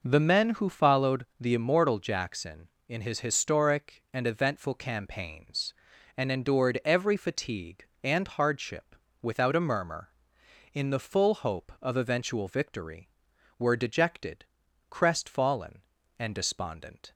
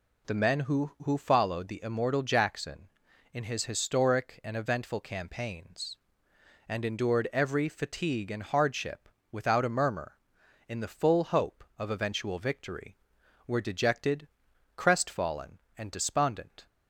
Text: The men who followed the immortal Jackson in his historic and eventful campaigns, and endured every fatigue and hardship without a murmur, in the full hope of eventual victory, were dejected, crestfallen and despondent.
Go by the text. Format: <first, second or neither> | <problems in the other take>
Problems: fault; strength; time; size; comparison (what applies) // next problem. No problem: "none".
first | says "who" twice; at 1.0 s // pauses between "hardship" and "without"; slight; at 9.0 s; 0.22 s long; slight in the first